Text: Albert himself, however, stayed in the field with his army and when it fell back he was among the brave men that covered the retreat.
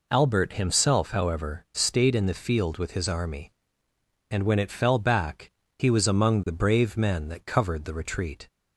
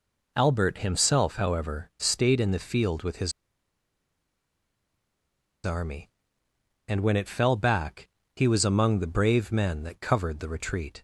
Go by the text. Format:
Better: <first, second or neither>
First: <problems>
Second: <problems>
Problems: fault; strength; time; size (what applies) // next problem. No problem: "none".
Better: first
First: pauses between "back" and "he"; slight; at 5.5 s; 0.28 s long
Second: pauses between "his" and "army"; strong; at 3.3 s; 2.3 s long // pauses between "back" and "he"; slight; at 8.0 s; 0.28 s long